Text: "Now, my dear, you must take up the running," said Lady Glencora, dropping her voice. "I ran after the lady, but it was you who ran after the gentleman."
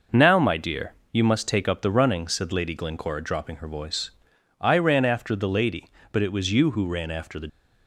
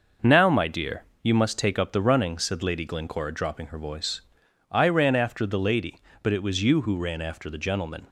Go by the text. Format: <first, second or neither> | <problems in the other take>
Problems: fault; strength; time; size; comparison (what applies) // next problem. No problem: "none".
second | stops before "gentleman"; at 7.4 s